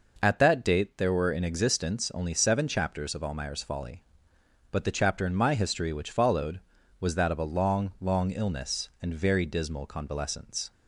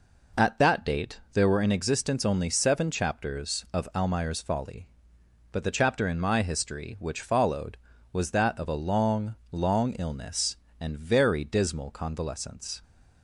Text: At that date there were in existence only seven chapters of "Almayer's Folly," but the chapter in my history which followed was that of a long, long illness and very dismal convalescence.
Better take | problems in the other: neither | none

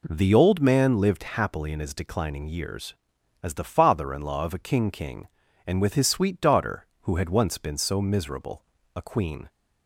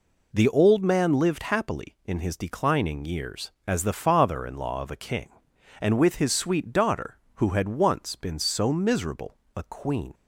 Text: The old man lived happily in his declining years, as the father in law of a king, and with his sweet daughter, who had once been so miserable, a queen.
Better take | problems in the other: second | says "king" twice; at 4.9 s

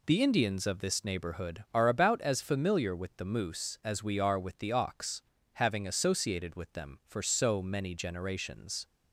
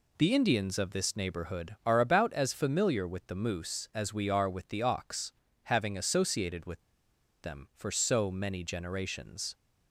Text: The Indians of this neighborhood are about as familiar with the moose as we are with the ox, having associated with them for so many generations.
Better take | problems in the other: first | pauses between "with" and "them"; noticeable; at 6.8 s; 0.60 s long

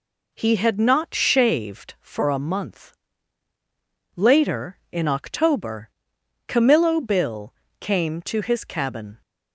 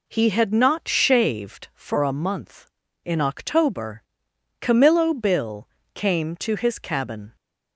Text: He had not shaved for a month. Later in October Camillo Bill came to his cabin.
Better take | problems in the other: first | skips "Later"; at 2.8 s // pauses between "October" and "Camillo"; noticeable; at 4.0 s; 0.60 s long; noticeable in the first // pauses between "Bill" and "came"; slight; at 5.6 s; 0.26 s long; slight in the first

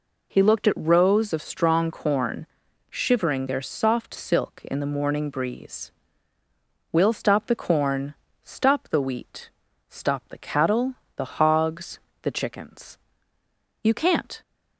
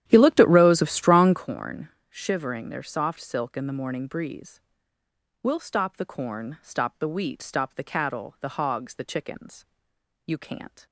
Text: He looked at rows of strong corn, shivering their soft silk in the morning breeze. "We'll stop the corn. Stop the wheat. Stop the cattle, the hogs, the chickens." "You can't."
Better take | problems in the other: first | starts louder than the rest; strong; until 1.5 s; 11 dB

